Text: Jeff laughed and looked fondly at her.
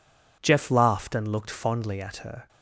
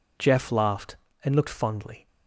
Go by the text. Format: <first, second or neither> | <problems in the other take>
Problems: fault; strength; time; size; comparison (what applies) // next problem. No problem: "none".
first | stops before "at her"; at 2.0 s